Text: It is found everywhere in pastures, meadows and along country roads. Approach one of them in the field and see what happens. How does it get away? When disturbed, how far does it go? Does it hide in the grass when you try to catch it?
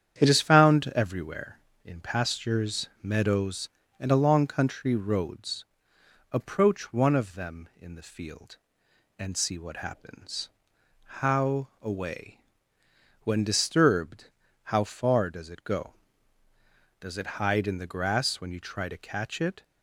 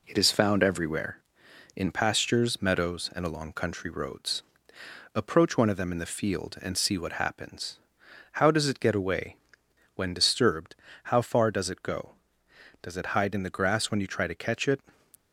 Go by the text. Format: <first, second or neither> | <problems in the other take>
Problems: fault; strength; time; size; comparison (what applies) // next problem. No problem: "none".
second | starts louder than the rest; strong; until 1.2 s; 9 dB // skips "does it get"; at 11.7 s